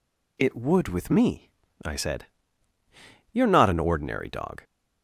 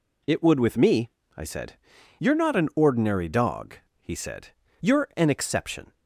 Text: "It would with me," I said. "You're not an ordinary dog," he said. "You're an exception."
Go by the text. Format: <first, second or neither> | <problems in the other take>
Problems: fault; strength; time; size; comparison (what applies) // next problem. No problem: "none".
second | stops before "he said You're an exception"; at 4.6 s